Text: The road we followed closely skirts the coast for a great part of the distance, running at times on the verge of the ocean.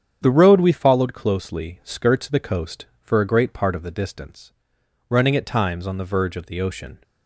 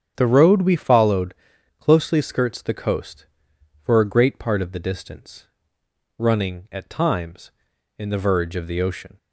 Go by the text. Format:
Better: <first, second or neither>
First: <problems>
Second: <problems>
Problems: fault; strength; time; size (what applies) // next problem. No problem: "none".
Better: first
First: starts louder than the rest; strong; until 1.2 s; 8.5 dB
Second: starts louder than the rest; strong; until 1.1 s; 8 dB // pauses between "followed" and "closely"; at 1.3 s; 0.44 s long // says "in" for "on"; at 7.9 s